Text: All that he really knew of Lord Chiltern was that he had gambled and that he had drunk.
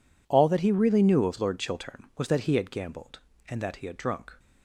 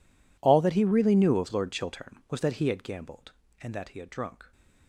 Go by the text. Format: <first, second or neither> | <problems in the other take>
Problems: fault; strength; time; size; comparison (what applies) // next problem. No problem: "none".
first | gets quieter; strong; throughout; 22.5 dB